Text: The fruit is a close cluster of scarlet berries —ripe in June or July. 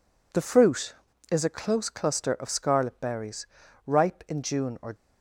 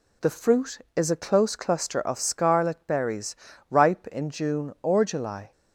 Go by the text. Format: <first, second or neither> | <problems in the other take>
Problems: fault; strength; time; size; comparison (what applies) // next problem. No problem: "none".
second | stops before "July"; at 4.9 s